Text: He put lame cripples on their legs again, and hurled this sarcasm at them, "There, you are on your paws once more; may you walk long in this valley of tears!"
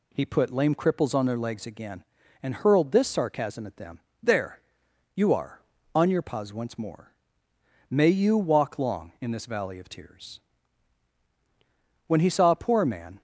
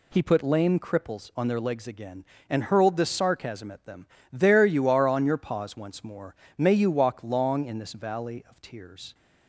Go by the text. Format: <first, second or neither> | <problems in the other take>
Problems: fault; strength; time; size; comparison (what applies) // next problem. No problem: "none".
second | goes on to say "When he saw a poor man"; noticeable; from 12.0 s on; 1.1 s long